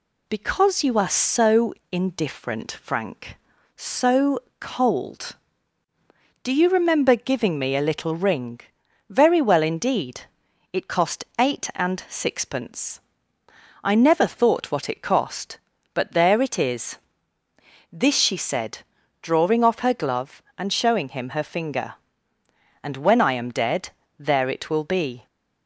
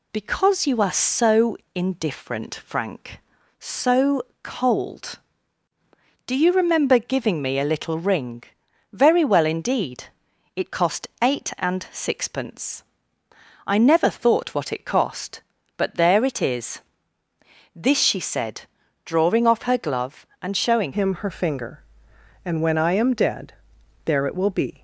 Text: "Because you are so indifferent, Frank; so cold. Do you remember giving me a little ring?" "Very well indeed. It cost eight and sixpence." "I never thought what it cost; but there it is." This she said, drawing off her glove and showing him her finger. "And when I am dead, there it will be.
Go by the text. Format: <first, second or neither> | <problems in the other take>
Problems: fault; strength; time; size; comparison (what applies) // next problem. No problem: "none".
first | pauses between "so" and "indifferent"; slight; at 1.5 s; 0.20 s long; slight in the first // pauses between "so" and "cold"; slight; at 4.2 s; 0.18 s long; slight in the first // pauses between "cost" and "eight"; slight; at 11.0 s; 0.16 s long; slight in the first // changes voice at "him"; from 20.9 s on; 3.9 s long